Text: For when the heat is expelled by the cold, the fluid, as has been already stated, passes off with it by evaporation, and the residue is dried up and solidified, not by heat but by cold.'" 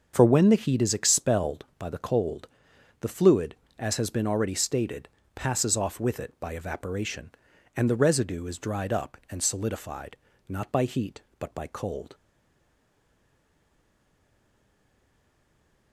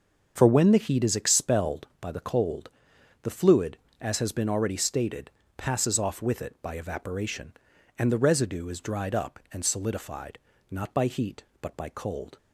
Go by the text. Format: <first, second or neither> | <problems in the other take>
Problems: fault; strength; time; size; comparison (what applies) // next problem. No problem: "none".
second | starts louder than the rest; until 1.1 s; 7 dB; also in the second // stays silent after the last word; strong; from 12.1 s on; 3.8 s long